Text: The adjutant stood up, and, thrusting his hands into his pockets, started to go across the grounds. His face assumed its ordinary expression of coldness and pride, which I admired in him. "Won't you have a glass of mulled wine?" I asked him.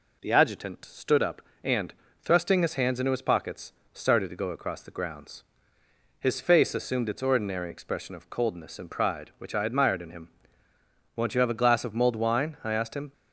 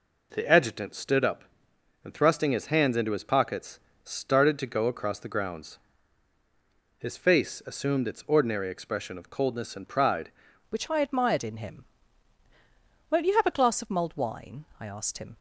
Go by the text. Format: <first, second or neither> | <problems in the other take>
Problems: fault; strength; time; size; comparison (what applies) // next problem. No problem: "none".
first | changes voice at "which"; from 10.6 s on; 4.7 s long